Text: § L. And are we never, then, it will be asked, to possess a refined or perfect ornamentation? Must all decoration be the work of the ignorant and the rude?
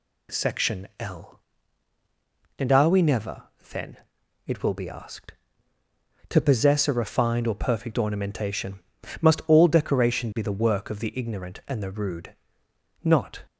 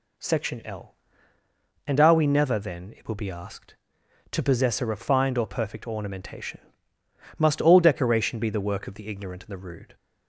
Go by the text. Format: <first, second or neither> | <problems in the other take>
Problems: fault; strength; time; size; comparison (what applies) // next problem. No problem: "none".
second | goes on to say "Not"; slight; from 13.0 s on; 0.40 s long